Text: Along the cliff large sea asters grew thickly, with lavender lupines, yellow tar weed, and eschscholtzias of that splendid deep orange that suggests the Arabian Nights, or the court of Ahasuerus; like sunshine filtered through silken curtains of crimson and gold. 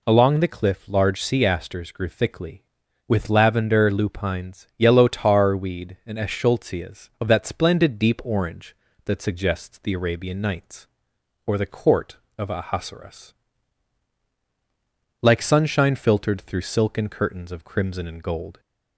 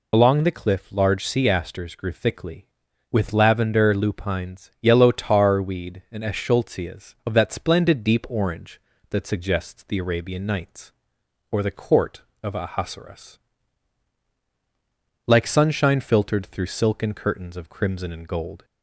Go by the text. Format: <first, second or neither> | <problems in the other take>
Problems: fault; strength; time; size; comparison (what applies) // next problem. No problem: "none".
first | loses the start of "Along"; at 0.1 s; 55 ms